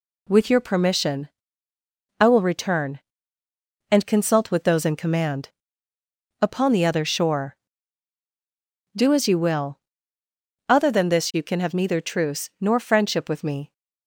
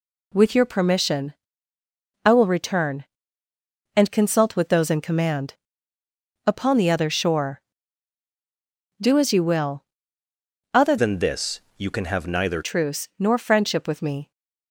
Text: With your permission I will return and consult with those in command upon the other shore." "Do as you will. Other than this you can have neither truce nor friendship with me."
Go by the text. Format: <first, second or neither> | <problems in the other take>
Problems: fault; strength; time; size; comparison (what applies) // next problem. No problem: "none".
first | pauses between "permission" and "I"; noticeable; at 1.3 s; 0.90 s long; noticeable in the first // pauses between "command" and "upon"; noticeable; at 5.5 s; 0.94 s long; noticeable in the first // changes voice from "than" to "neither"; from 10.9 to 12.6 s; 1.7 s long // pauses between "this" and "you"; slight; at 11.5 s; 0.18 s long